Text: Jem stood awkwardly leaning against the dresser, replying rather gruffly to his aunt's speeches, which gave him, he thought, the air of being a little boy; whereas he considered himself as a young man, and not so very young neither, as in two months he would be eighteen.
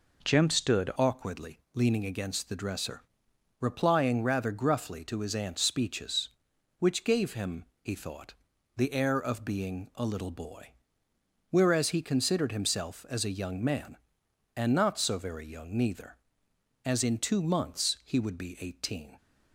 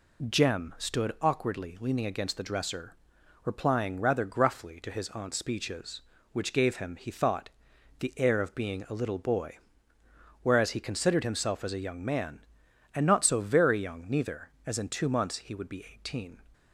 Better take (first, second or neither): second